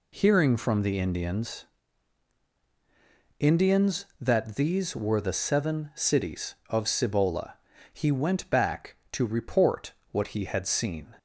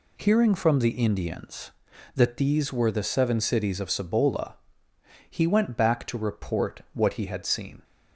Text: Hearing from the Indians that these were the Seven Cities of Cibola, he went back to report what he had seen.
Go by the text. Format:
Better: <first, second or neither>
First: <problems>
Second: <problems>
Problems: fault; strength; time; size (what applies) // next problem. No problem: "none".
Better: second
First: says "Indians" twice; at 3.3 s // pauses between "report" and "what"; slight; at 9.9 s; 0.18 s long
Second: none